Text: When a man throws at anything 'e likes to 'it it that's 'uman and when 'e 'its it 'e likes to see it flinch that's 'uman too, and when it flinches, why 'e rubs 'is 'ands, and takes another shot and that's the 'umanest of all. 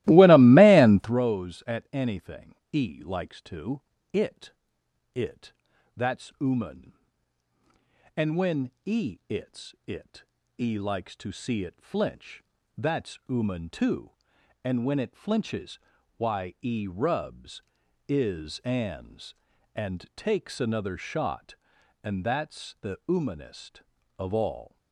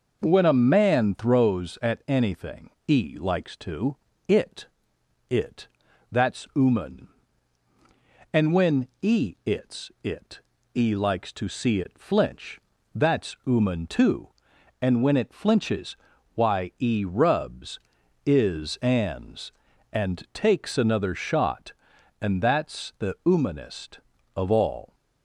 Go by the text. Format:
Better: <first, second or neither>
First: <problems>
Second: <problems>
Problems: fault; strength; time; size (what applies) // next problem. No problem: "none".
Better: second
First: starts louder than the rest; strong; until 1.2 s; 17.5 dB // pauses between "anything" and "e"; slight; at 2.5 s; 0.16 s long // pauses between "to" and "it"; slight; at 3.8 s; 0.30 s long // pauses between "it" and "it"; noticeable; at 4.5 s; 0.64 s long // pauses between "it" and "that's"; at 5.5 s; 0.44 s long // pauses between "when" and "e"; slight; at 8.7 s; 0.16 s long // pauses between "it" and "e"; slight; at 10.2 s; 0.34 s long // pauses between "flinch" and "that's"; slight; at 12.4 s; 0.36 s long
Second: pauses between "anything" and "e"; slight; at 2.7 s; 0.16 s long // pauses between "to" and "it"; slight; at 3.9 s; 0.30 s long // pauses between "it" and "it"; noticeable; at 4.6 s; 0.64 s long // pauses between "it" and "that's"; at 5.6 s; 0.44 s long // pauses between "when" and "e"; slight; at 8.8 s; 0.16 s long // pauses between "it" and "e"; slight; at 10.4 s; 0.34 s long // pauses between "flinch" and "that's"; slight; at 12.6 s; 0.36 s long